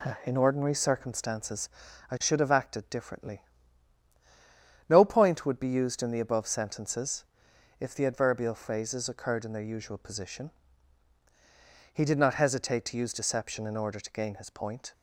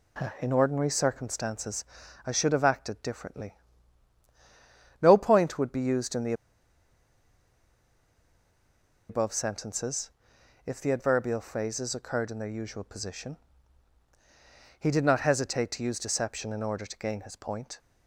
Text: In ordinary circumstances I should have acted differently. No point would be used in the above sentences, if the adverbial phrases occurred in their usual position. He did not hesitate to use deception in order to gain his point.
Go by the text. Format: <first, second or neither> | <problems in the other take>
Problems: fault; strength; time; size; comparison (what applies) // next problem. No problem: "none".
first | pauses between "circumstances" and "I"; at 1.8 s; 0.40 s long; also in the first // pauses between "the" and "above"; strong; at 6.3 s; 2.7 s long